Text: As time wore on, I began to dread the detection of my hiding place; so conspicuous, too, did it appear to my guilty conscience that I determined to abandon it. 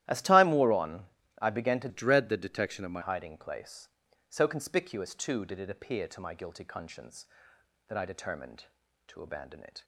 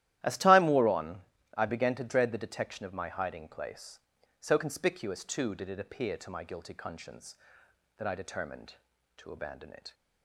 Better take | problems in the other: second | starts louder than the rest; strong; until 1.4 s; 13.5 dB; strong in the second // changes voice from "dread" to "my"; from 1.8 to 3.0 s; 1.2 s long

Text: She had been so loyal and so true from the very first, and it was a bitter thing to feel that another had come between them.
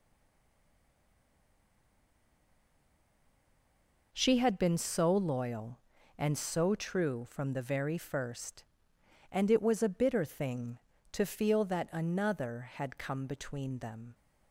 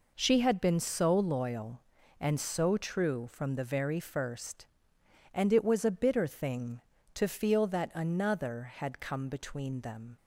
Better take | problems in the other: second | stays silent before the first word; strong; until 4.1 s; 4.1 s long

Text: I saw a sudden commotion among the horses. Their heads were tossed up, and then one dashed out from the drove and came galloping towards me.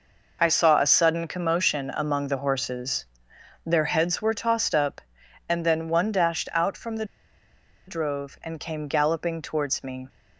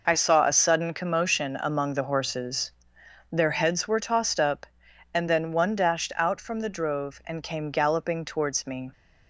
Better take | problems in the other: second | pauses between "the" and "drove"; noticeable; at 7.0 s; 0.83 s long

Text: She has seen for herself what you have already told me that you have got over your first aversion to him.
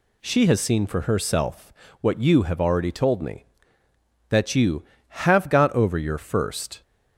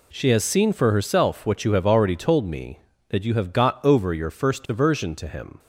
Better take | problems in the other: second | pauses between "herself" and "what"; slight; at 1.7 s; 0.30 s long // stops before "aversion to him"; at 6.8 s

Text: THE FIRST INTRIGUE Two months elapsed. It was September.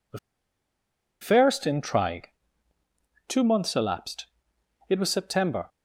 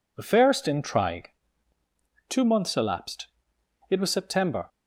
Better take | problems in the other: second | pauses between "THE" and "FIRST"; at 0.1 s; 1.0 s long // pauses between "INTRIGUE" and "Two"; at 2.2 s; 1.0 s long; also in the second

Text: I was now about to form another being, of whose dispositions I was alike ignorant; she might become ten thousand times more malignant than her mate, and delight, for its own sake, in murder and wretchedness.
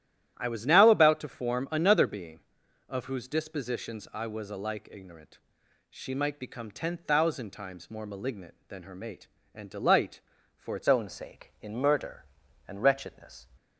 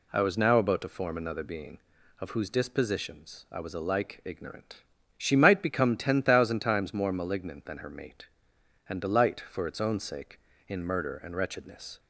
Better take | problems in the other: second | starts louder than the rest; strong; until 1.3 s; 12.5 dB // changes voice at "own"; from 10.8 s on; 2.6 s long

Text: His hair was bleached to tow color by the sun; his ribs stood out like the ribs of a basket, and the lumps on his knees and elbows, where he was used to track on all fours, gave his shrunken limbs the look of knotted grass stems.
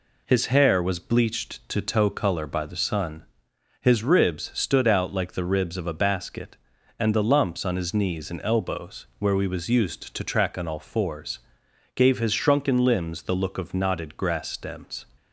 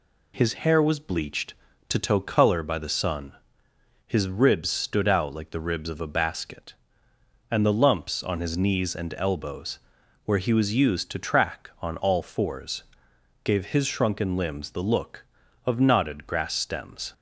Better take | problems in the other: second | says "we" for "he"; at 9.3 s

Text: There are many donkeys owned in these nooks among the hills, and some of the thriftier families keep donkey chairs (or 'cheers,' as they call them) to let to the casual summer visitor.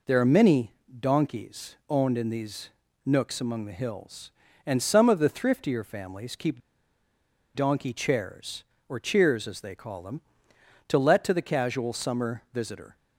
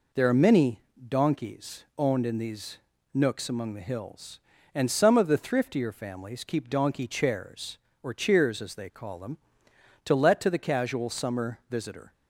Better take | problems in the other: second | pauses between "many" and "donkeys"; slight; at 0.7 s; 0.28 s long; slight in the second // pauses between "these" and "nooks"; slight; at 2.6 s; 0.36 s long; slight in the second // pauses between "keep" and "donkey"; noticeable; at 6.5 s; 0.94 s long

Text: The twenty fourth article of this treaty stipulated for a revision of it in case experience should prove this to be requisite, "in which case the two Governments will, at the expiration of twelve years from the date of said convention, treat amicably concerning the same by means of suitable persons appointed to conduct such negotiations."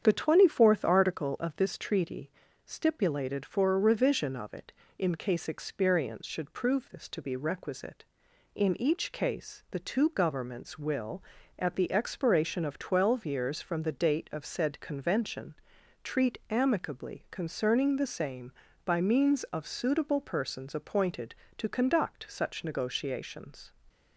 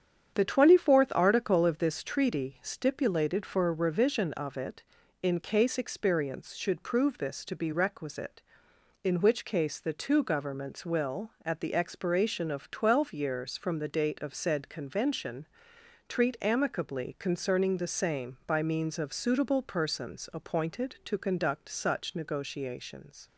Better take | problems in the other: second | starts louder than the rest; strong; until 1.0 s; 8 dB; strong in the second // pauses between "treaty" and "stipulated"; slight; at 2.2 s; 0.36 s long // says "each" for "which"; at 8.8 s

